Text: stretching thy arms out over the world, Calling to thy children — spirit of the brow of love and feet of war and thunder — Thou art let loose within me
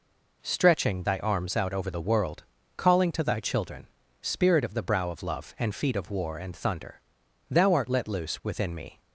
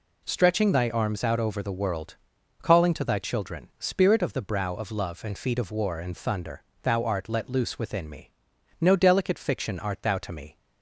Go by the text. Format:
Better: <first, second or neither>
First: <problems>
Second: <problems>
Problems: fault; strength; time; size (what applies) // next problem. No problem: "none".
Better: first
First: none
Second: goes on to say "No delicate fiction art thou to me"; strong; from 8.7 s on; 1.7 s long